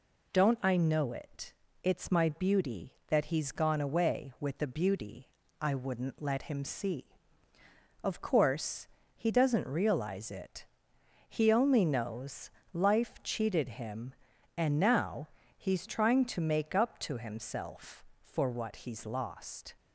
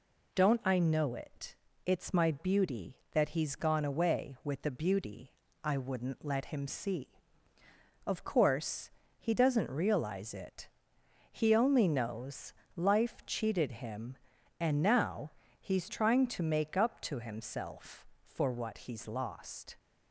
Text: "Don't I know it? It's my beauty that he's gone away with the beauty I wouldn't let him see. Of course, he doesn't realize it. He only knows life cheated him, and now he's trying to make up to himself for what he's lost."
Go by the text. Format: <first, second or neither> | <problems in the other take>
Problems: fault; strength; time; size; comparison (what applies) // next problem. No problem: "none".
neither | pauses between "beauty" and "I"; slight; the same in both // pauses between "knows" and "life"; slight; the same in both // pauses between "now" and "he's"; slight; the same in both